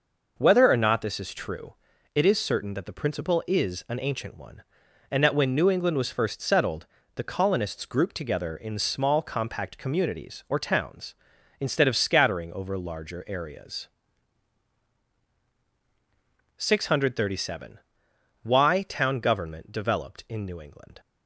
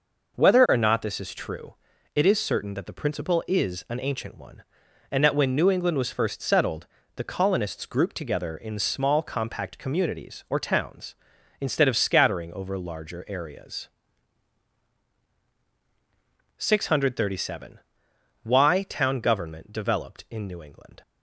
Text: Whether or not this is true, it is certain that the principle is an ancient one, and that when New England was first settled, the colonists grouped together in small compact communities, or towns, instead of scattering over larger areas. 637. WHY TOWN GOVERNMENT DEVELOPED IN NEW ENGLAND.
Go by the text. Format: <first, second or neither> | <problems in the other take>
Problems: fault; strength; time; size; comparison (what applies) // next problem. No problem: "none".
neither | none